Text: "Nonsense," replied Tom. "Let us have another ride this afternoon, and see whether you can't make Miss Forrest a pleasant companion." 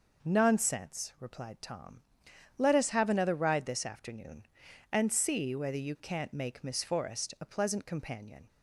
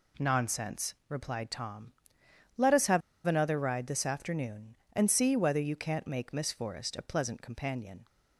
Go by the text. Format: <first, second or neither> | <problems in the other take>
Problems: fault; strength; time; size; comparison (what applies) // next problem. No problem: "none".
first | pauses between "have" and "another"; slight; at 3.0 s; 0.26 s long